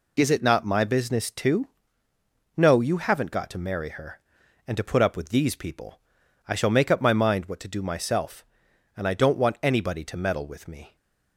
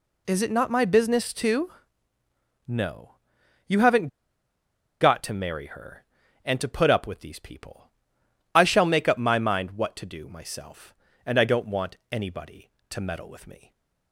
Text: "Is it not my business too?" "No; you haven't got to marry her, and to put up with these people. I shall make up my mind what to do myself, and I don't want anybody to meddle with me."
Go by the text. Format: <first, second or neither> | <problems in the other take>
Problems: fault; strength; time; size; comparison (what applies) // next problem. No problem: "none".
first | pauses between "haven't" and "got"; noticeable; at 4.0 s; 0.93 s long // pauses between "want" and "anybody"; slight; at 11.9 s; 0.16 s long